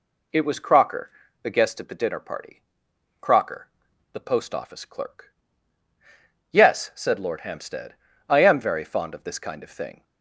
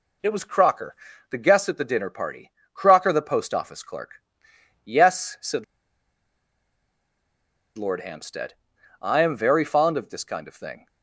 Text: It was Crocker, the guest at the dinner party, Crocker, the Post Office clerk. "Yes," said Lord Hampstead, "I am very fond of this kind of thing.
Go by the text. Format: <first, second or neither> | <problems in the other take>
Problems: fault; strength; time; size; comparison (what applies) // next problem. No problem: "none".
first | pauses between "said" and "Lord"; strong; at 5.6 s; 2.1 s long